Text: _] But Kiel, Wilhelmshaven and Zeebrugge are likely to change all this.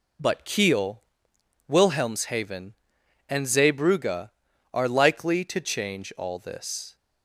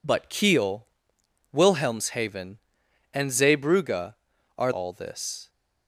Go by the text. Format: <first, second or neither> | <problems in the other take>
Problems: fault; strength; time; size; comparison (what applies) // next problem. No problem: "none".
first | skips "likely to change"; at 4.7 s